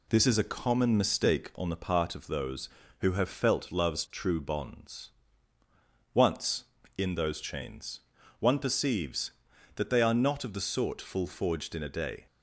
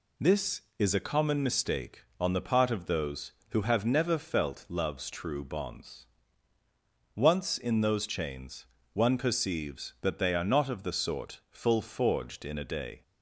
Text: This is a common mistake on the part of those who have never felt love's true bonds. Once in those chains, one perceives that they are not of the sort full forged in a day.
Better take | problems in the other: second | skips "never"; at 3.2 s

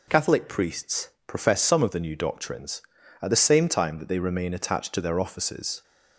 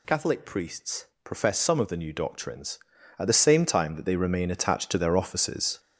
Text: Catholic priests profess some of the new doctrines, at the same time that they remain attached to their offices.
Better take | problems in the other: first | gets louder; throughout; 7 dB // pauses between "priests" and "profess"; slight; at 1.0 s; 0.18 s long; slight in the first

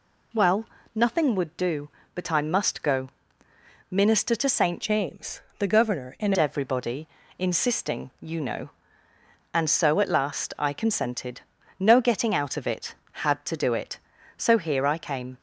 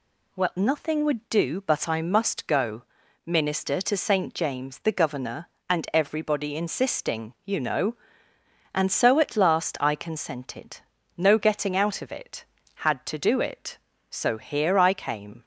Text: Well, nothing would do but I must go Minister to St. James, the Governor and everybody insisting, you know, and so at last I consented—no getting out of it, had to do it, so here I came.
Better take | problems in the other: second | pauses between "go" and "Minister"; noticeable; at 3.0 s; 0.80 s long; also in the second // changes voice from "James" to "and"; from 4.8 to 6.3 s; 1.5 s long // pauses between "everybody" and "insisting"; slight; at 7.0 s; 0.32 s long

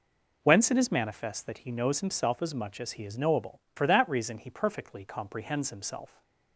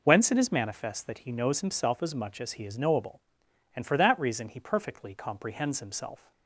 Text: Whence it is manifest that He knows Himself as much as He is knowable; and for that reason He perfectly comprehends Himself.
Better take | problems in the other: second | skips "and"; at 3.6 s

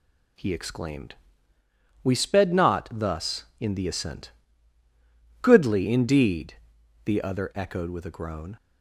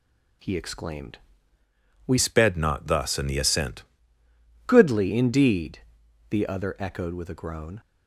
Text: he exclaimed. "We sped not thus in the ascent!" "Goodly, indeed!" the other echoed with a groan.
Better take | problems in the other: first | changes voice from "sped" to "ascent"; from 2.1 to 3.8 s; 1.7 s long

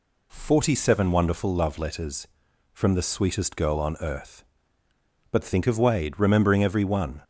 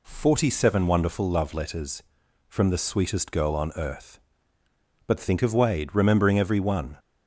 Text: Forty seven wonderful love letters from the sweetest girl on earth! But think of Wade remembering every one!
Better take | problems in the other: neither | none

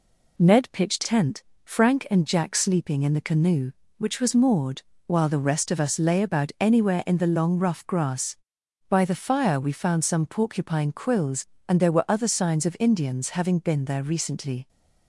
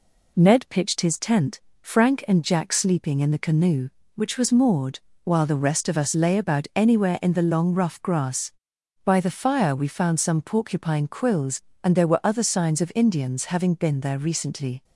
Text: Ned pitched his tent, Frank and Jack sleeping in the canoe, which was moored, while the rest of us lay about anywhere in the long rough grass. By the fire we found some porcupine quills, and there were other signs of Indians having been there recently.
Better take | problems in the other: second | skips "his"; at 1.0 s

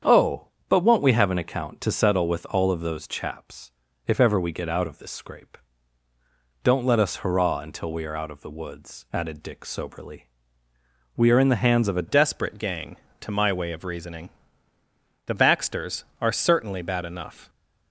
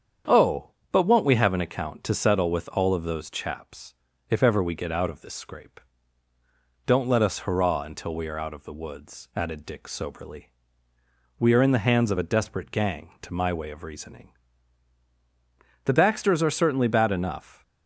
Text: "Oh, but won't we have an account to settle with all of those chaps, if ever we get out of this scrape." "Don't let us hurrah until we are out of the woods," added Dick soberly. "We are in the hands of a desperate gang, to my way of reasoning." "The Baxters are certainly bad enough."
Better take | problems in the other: second | starts louder than the rest; strong; until 1.2 s; 8 dB; strong in the second // changes voice at "desperate"; from 12.0 s on; 5.4 s long

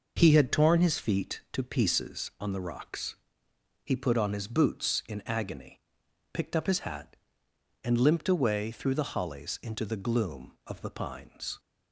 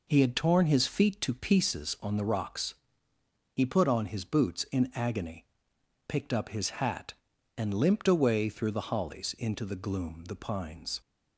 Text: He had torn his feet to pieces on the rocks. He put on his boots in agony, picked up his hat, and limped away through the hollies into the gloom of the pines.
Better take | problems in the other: first | skips "of"; at 10.2 s

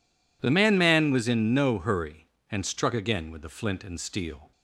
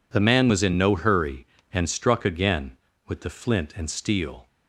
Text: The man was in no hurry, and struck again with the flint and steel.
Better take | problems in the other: second | says "man" twice; at 0.7 s

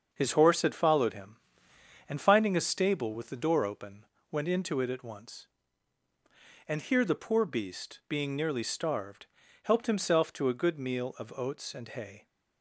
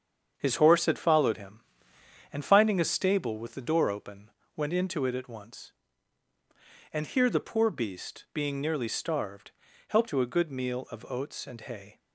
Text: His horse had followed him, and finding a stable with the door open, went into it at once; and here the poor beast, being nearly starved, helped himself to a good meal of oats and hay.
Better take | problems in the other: first | starts louder than the rest; strong; until 1.3 s; 7.5 dB; also in the first // skips "himself"; at 10.0 s

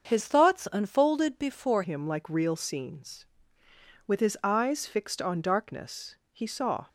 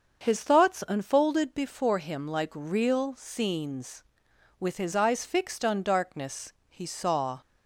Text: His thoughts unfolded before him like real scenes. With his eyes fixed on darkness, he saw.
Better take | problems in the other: second | starts louder than the rest; until 1.1 s; 6.5 dB; also in the second // changes voice at "him"; from 1.8 s on; 5.0 s long

